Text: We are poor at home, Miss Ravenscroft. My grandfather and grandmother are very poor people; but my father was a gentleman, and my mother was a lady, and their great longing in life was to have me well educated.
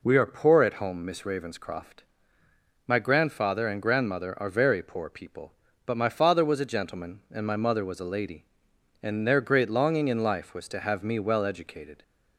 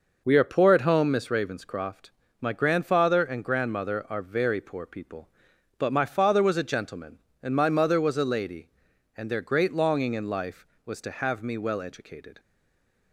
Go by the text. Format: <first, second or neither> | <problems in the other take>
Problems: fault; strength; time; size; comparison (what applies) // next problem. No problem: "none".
first | stays silent after the last word; slight; from 12.3 s on; 0.8 s long